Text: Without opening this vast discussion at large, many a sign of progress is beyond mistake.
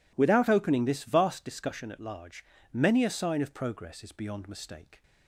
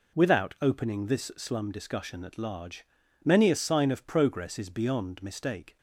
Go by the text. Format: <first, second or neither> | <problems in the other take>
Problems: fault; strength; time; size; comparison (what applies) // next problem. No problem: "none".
first | says "slum" for "vast"; at 1.3 s